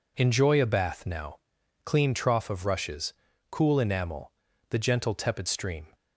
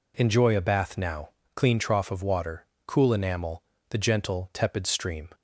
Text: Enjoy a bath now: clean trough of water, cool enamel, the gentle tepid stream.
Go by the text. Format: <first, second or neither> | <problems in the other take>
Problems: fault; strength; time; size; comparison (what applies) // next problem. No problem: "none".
second | says "rushes" for "water"; at 2.6 s